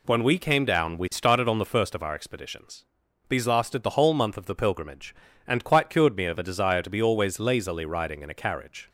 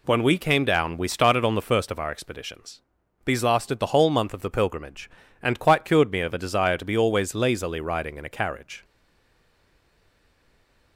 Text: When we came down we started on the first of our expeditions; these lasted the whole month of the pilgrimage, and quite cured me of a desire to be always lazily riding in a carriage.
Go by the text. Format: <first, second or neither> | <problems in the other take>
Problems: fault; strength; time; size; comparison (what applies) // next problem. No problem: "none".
first | stays silent after the last word; from 8.8 s on; 2.1 s long